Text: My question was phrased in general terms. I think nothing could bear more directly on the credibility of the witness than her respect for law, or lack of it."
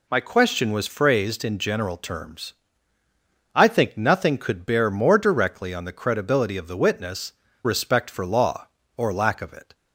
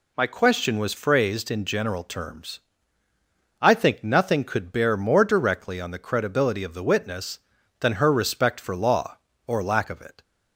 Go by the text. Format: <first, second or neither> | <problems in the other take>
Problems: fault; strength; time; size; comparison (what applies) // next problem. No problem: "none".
second | skips "than her"; at 7.4 s